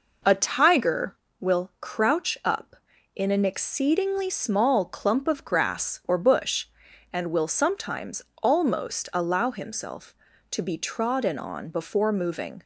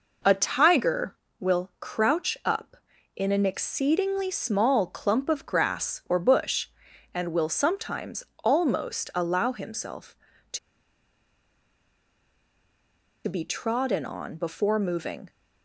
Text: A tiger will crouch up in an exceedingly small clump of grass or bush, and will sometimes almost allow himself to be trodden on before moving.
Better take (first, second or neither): first